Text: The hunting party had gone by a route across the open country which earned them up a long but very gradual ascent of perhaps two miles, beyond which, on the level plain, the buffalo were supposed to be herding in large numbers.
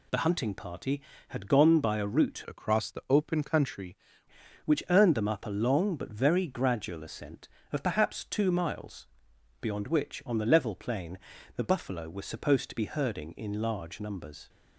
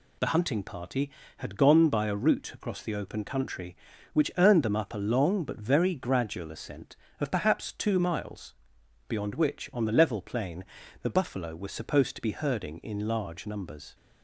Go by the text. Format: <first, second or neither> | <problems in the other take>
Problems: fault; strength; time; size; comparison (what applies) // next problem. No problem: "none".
second | changes voice from "across" to "country"; from 2.4 to 3.9 s; 1.5 s long